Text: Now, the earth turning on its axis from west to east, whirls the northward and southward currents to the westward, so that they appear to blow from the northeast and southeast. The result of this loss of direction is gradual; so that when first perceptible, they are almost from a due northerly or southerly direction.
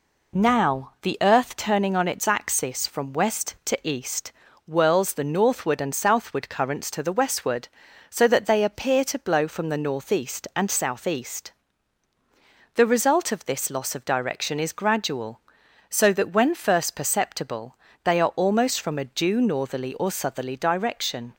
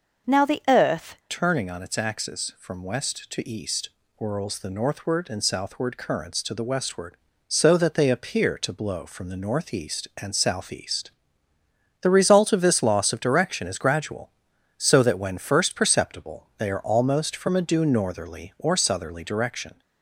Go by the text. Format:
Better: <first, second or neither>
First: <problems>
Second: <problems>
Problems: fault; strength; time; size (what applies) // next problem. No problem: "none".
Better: first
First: none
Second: changes voice at "turning"; from 1.2 s on; 18.6 s long